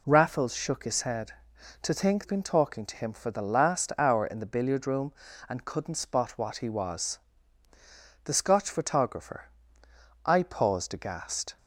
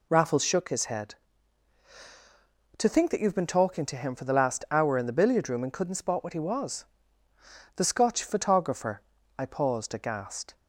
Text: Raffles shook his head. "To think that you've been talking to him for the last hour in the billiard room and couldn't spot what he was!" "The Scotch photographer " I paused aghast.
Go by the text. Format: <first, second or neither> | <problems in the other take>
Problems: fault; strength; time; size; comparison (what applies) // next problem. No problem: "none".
second | skips "that you've"; at 2.2 s